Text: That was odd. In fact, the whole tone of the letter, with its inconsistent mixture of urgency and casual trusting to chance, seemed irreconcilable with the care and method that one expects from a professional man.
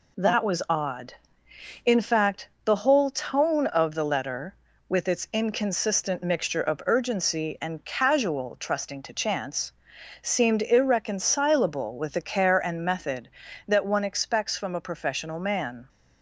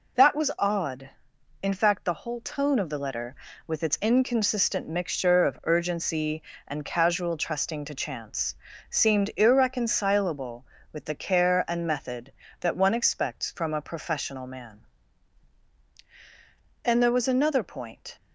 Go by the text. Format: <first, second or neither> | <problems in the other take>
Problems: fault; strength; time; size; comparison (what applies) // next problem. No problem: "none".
first | goes on to say "And there was another point"; from 16.8 s on; 1.3 s long